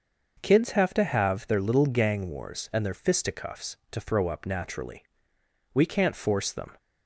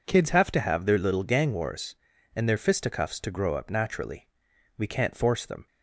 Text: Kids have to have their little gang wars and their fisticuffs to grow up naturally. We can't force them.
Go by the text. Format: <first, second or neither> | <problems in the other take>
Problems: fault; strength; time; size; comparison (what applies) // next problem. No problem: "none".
second | starts louder than the rest; noticeable; until 1.4 s; 6 dB // says "throw" for "grow"; at 4.0 s